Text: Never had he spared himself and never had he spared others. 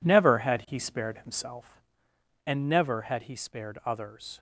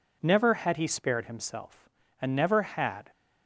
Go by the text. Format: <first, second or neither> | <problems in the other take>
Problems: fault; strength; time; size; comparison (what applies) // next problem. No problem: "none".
first | stops before "he spared others"; at 3.1 s